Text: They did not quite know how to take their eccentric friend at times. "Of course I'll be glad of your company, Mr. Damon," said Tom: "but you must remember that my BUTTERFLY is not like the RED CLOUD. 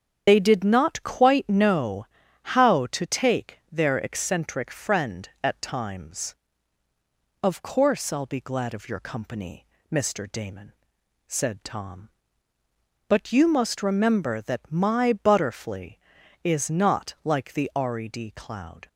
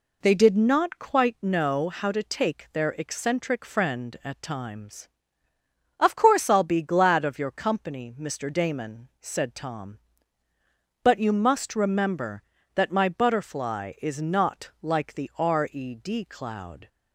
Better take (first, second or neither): second